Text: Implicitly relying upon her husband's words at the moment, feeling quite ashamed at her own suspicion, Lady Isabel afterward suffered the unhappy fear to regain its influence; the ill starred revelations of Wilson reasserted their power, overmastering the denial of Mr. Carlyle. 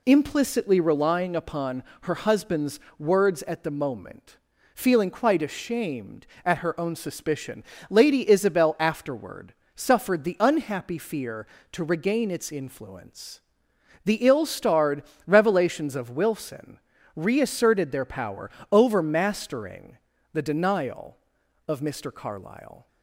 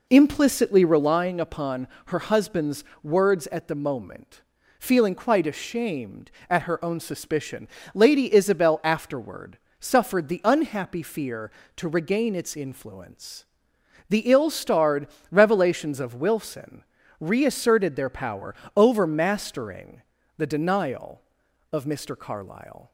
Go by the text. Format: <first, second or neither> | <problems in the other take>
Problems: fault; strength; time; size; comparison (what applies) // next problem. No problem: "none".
first | starts louder than the rest; noticeable; until 1.3 s; 4 dB // pauses between "upon" and "her"; slight; at 1.8 s; 0.18 s long; slight in the first // pauses between "husband's" and "words"; slight; at 2.8 s; 0.20 s long; slight in the first // pauses between "afterward" and "suffered"; slight; at 9.5 s; 0.24 s long; slight in the first // pauses between "starred" and "revelations"; slight; at 15.0 s; 0.22 s long; slight in the first // pauses between "Wilson" and "reasserted"; slight; at 16.8 s; 0.36 s long; slight in the first // pauses between "overmastering" and "the"; slight; at 20.0 s; 0.34 s long; slight in the first